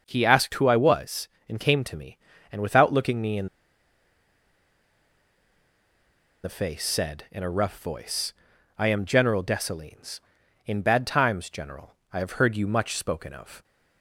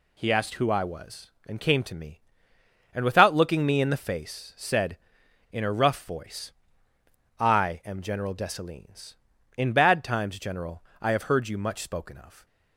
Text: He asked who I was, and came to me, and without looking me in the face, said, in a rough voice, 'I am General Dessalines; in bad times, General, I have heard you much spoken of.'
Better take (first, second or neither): second